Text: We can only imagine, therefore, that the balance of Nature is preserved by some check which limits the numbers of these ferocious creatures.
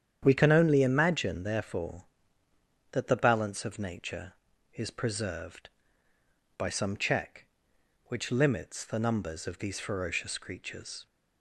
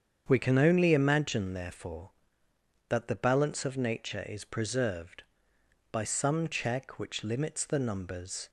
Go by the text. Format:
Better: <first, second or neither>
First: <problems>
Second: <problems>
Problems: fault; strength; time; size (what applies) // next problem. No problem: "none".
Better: first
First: starts louder than the rest; strong; until 1.2 s; 9 dB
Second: starts louder than the rest; strong; until 1.2 s; 7.5 dB // stops before "of these ferocious creatures"; at 8.4 s